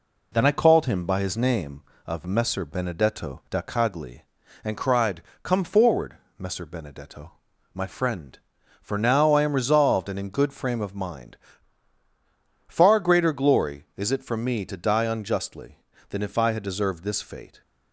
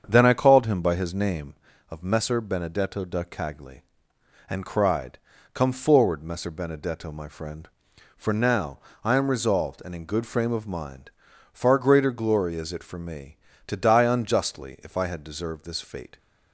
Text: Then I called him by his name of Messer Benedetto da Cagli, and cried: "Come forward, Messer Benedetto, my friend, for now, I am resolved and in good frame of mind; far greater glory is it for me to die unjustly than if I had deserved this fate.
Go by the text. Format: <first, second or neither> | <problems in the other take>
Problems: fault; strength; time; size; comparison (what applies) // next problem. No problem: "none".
first | starts louder than the rest; strong; until 1.0 s; 7.5 dB // skips "than"; at 14.7 s